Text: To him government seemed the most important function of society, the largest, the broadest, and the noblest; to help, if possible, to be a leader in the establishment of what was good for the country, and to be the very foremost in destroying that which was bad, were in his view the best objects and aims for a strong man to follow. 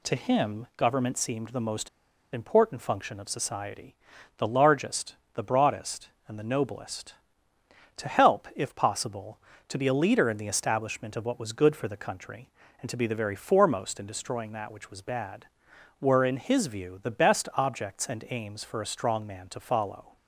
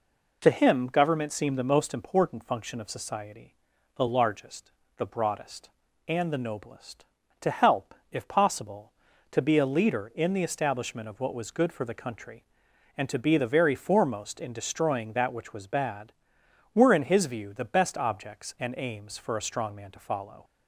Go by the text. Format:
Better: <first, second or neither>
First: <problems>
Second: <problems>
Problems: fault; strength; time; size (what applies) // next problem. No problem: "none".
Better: second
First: pauses between "most" and "important"; at 1.8 s; 0.44 s long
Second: none